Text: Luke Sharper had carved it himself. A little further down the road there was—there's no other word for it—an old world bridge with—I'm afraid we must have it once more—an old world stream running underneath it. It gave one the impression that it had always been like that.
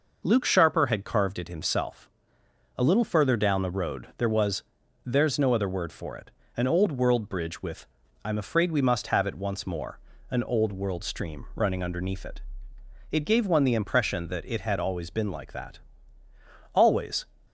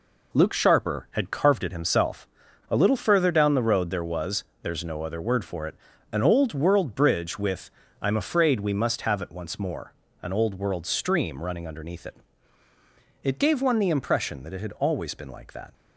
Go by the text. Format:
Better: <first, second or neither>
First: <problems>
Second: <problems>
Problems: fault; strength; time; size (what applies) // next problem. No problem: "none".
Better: second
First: goes on to say "Always"; from 16.7 s on; 0.50 s long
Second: none